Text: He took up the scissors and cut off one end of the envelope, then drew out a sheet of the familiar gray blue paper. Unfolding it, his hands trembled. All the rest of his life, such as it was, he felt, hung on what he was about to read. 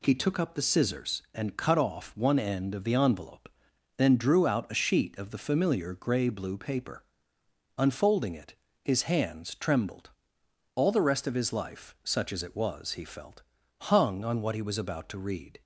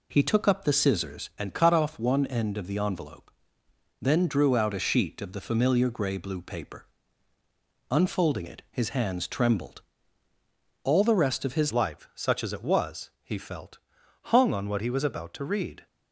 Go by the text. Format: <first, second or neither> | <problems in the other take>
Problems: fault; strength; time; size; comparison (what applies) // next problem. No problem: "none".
first | changes voice at "life"; from 11.7 s on; 4.1 s long